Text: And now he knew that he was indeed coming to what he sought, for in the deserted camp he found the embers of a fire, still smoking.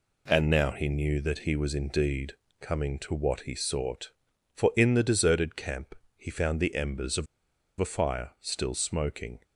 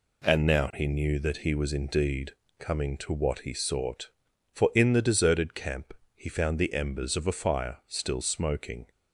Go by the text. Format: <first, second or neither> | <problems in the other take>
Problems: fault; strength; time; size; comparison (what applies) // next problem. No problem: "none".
second | pauses between "indeed" and "coming"; slight; at 2.3 s; 0.28 s long; slight in the second // pauses between "camp" and "he"; slight; at 5.9 s; 0.22 s long; slight in the second // pauses between "of" and "a"; noticeable; at 7.2 s; 0.53 s long